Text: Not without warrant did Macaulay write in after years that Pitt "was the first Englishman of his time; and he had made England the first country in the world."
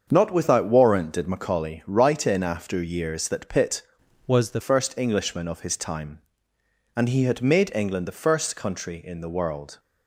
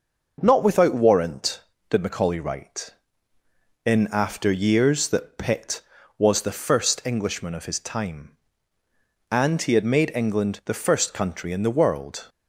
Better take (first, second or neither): second